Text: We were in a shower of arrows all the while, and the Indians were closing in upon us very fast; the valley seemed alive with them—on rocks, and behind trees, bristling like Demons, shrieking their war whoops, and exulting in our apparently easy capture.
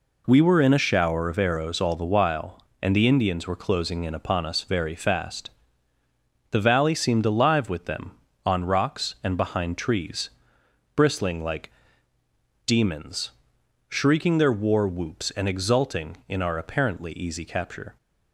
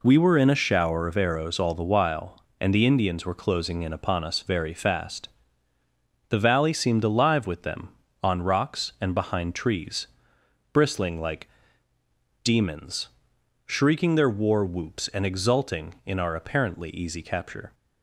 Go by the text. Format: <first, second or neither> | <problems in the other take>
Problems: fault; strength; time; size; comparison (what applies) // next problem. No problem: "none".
neither | pauses between "like" and "Demons"; noticeable; the same in both